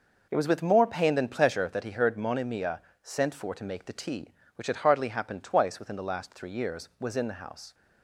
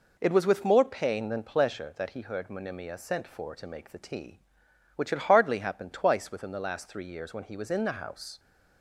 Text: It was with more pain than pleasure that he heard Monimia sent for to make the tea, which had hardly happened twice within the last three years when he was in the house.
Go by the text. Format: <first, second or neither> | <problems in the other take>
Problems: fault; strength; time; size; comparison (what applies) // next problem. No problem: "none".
second | pauses between "Monimia" and "sent"; slight; at 2.7 s; 0.24 s long // skips "when he"; at 6.9 s